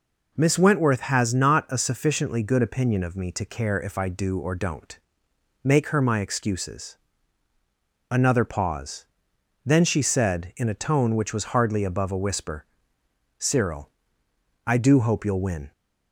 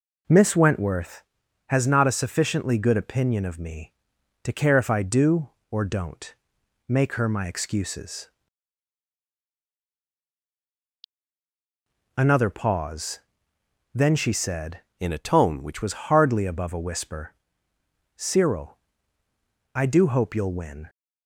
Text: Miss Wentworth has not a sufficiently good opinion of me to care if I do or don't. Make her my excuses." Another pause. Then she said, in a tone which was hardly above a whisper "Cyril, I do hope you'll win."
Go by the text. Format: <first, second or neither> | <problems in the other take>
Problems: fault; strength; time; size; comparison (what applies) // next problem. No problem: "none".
first | changes voice from "in" to "which"; from 14.9 to 15.8 s; 0.9 s long // pauses between "whisper" and "Cyril"; noticeable; at 17.3 s; 0.82 s long; noticeable in the first